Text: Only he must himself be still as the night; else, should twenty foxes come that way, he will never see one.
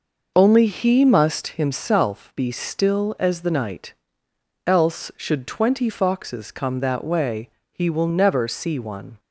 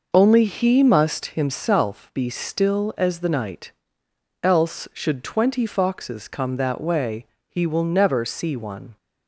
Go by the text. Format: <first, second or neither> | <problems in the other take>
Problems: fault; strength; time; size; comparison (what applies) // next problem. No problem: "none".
neither | none